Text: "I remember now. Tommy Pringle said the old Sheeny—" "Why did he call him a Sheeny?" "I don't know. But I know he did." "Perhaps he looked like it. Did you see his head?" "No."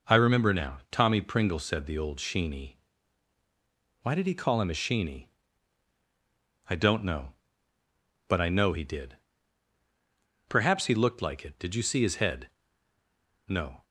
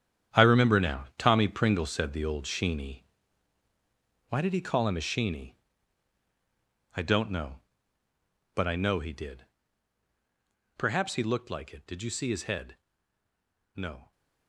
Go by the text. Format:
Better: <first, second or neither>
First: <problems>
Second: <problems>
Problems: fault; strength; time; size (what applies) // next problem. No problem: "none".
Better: first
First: none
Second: gets quieter; strong; throughout; 13 dB